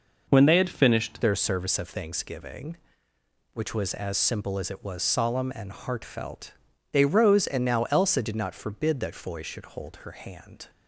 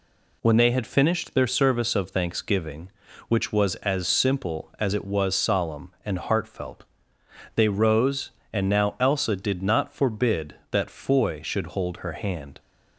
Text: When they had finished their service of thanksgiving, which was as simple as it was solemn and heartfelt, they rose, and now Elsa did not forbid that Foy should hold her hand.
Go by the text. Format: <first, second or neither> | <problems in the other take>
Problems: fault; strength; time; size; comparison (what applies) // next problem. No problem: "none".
second | changes voice at "their"; from 1.2 s on; 9.4 s long